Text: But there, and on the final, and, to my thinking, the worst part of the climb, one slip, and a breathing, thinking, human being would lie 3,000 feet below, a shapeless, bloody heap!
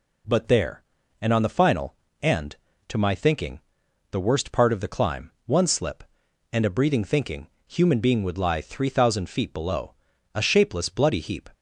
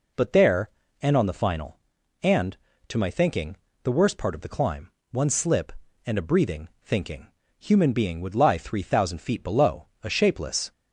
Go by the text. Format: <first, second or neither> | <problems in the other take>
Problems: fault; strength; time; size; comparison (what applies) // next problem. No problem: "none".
first | stops before "bloody heap"; at 10.7 s